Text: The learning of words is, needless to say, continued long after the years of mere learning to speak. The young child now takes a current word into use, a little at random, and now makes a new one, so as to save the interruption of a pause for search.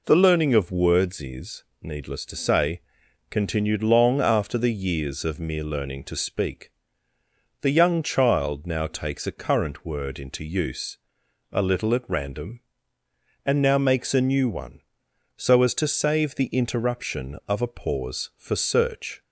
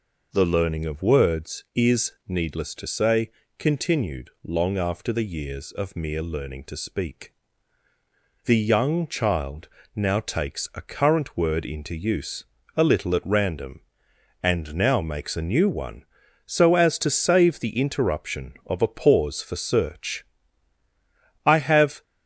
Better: first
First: none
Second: pauses between "child" and "now"; slight; at 9.6 s; 0.26 s long // goes on to say "I have"; from 21.4 s on; 0.58 s long

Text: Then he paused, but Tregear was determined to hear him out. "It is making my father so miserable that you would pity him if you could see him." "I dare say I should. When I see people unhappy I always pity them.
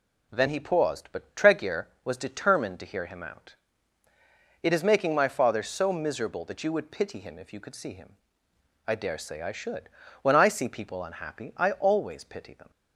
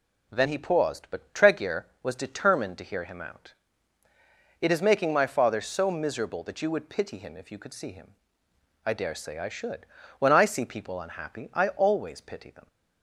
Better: neither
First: none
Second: none

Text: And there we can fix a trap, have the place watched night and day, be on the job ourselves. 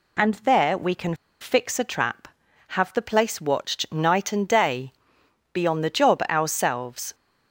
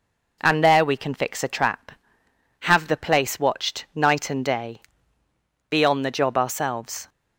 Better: second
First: pauses between "can" and "fix"; slight; at 1.1 s; 0.26 s long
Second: none

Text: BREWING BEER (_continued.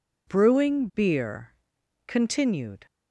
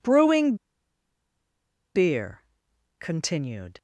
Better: first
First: none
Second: pauses between "BREWING" and "BEER"; strong; at 0.5 s; 1.4 s long

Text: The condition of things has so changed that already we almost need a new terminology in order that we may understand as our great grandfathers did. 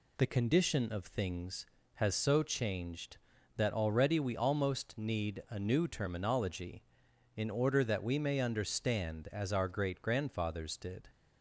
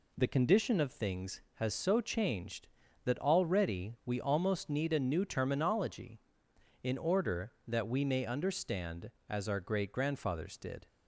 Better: neither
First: none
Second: none

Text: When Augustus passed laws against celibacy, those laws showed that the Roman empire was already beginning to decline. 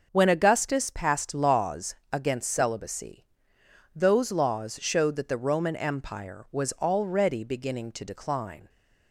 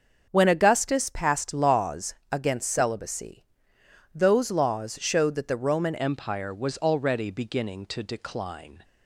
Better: first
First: pauses between "laws" and "against"; slight; at 1.9 s; 0.16 s long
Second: starts louder than the rest; until 1.3 s; 6.5 dB // pauses between "laws" and "against"; slight; at 2.1 s; 0.16 s long // changes voice at "empire"; from 5.9 s on; 2.9 s long

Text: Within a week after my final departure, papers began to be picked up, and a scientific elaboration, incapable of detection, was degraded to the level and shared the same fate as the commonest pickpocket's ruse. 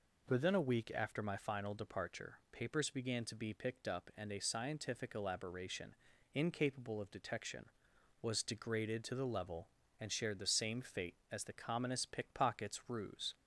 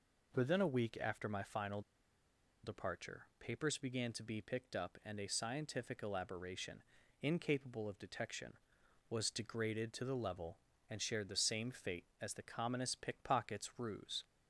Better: first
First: none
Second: pauses between "final" and "departure"; noticeable; at 1.8 s; 0.82 s long

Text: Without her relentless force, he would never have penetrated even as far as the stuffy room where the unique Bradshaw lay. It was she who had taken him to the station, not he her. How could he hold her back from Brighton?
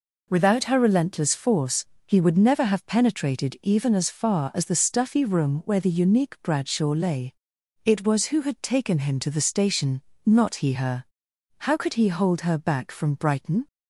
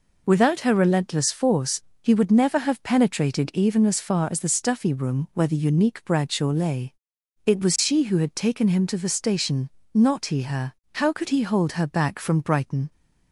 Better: second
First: skips "she"; at 8.2 s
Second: none

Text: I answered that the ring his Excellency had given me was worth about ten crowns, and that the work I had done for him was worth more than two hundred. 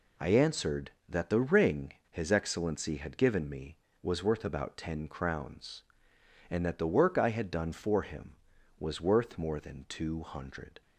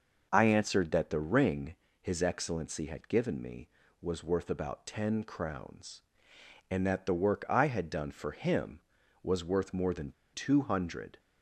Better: first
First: pauses between "ring" and "his"; slight; at 1.9 s; 0.15 s long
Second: pauses between "ring" and "his"; slight; at 1.7 s; 0.26 s long // pauses between "than" and "two"; slight; at 10.1 s; 0.22 s long

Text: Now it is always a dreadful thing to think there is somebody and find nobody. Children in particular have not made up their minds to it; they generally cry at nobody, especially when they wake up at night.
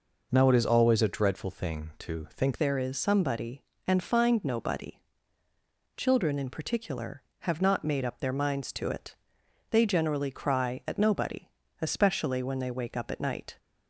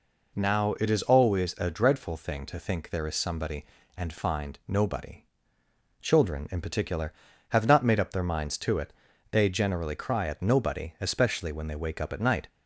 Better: second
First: changes voice at "there"; from 2.5 s on; 11.0 s long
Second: none

